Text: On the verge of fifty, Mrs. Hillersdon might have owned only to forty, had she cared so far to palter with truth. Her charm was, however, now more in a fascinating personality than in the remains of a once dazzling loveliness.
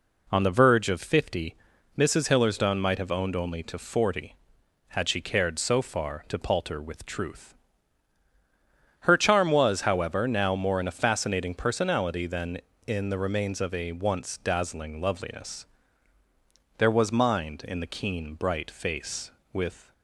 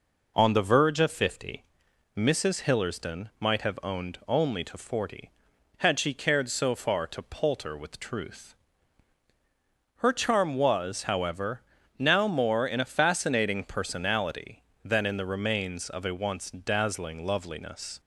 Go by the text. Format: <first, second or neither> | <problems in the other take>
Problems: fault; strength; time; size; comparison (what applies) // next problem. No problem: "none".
second | goes on to say "There was mind in the keen bright face with"; strong; from 16.7 s on; 3.1 s long